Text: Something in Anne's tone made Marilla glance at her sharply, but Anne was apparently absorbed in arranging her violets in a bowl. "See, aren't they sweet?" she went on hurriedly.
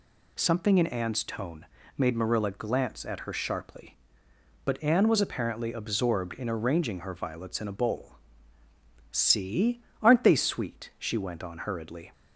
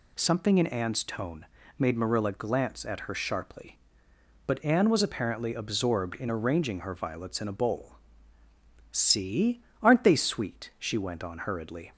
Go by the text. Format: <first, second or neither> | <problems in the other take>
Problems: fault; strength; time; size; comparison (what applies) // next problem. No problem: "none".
neither | pauses between "tone" and "made"; slight; the same in both